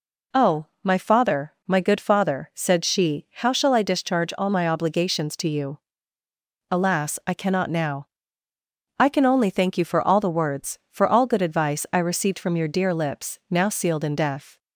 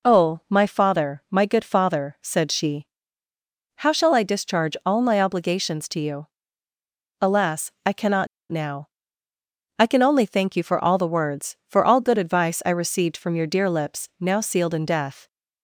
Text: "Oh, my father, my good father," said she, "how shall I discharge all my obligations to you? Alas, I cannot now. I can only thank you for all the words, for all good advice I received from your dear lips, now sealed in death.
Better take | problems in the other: first | pauses between "cannot" and "now"; slight; at 8.2 s; 0.23 s long

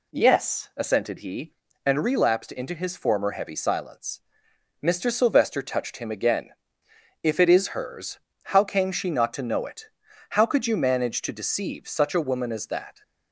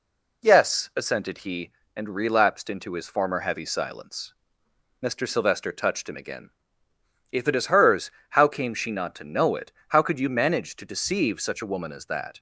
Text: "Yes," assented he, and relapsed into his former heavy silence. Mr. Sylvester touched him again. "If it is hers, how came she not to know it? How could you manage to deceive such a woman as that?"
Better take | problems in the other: neither | none

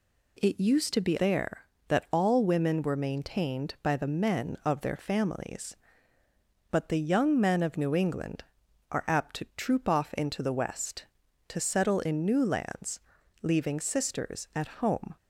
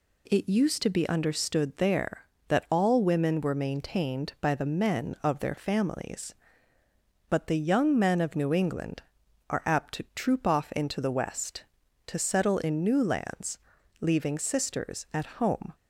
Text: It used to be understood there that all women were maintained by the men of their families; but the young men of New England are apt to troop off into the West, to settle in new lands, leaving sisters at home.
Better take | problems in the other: second | skips "understood"; at 1.1 s

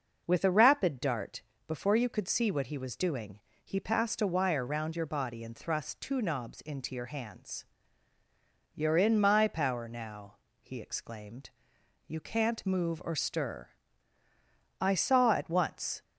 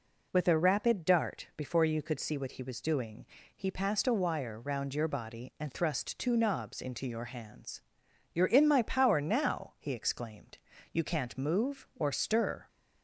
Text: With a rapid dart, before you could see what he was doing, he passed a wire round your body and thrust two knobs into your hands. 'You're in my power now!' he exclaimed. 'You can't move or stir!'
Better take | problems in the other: second | goes on to say "I saw at once"; noticeable; from 14.7 s on; 1.2 s long

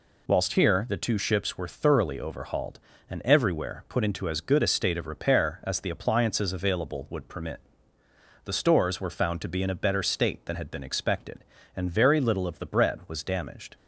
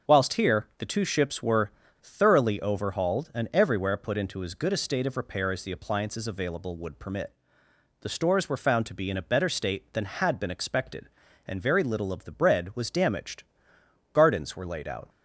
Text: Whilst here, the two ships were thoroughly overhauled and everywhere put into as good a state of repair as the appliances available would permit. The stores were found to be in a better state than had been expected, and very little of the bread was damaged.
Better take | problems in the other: first | starts louder than the rest; until 1.1 s; 6 dB // pauses between "were" and "thoroughly"; slight; at 1.7 s; 0.31 s long // goes on to say "Gardens were laid out"; noticeable; from 14.1 s on; 0.96 s long

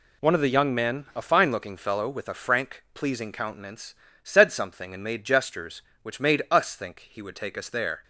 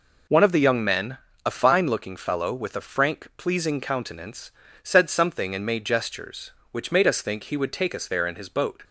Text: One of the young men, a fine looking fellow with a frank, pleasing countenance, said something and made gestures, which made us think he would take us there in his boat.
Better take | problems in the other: second | stops before "in his boat"; at 8.0 s

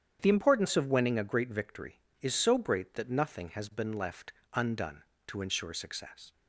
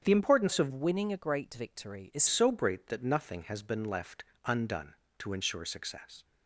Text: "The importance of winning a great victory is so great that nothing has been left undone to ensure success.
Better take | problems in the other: first | starts louder than the rest; strong; until 1.0 s; 8 dB; strong in the first // changes voice from "winning" to "is"; from 0.7 to 2.2 s; 1.5 s long // pauses between "left" and "undone"; slight; at 4.2 s; 0.22 s long; slight in the first

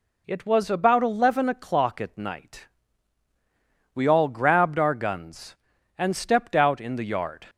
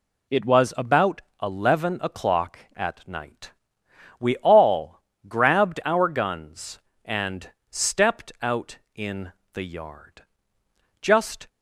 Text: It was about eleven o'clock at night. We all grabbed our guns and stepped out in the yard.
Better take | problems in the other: first | pauses between "about" and "eleven"; slight; at 1.2 s; 0.20 s long // pauses between "all" and "grabbed"; slight; at 4.9 s; 0.26 s long // pauses between "and" and "stepped"; slight; at 7.4 s; 0.20 s long // pauses between "in" and "the"; slight; at 9.3 s; 0.22 s long // goes on to say "Just"; slight; from 10.9 s on; 0.48 s long

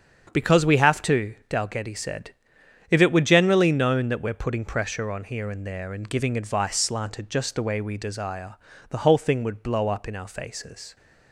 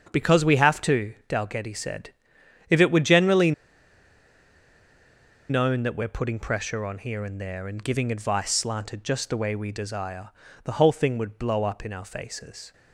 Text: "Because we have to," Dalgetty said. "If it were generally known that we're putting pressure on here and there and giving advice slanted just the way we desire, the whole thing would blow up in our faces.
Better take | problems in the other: first | starts louder than the rest; strong; until 1.1 s; 7.5 dB; strong in the first // pauses between "generally" and "known"; strong; at 3.5 s; 1.9 s long

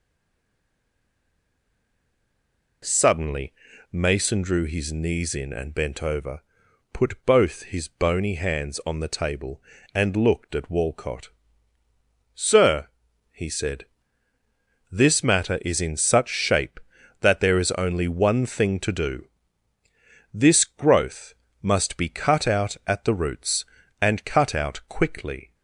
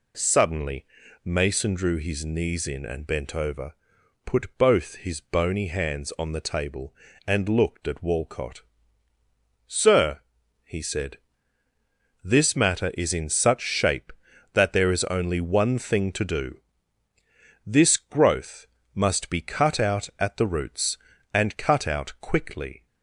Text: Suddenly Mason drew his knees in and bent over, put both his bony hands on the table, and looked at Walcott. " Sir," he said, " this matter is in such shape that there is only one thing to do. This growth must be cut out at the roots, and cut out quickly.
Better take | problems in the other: second | stays silent before the first word; strong; until 2.8 s; 2.8 s long // pauses between "Suddenly" and "Mason"; at 3.5 s; 0.38 s long; also in the second // pauses between "growth" and "must"; slight; at 21.3 s; 0.28 s long; slight in the second

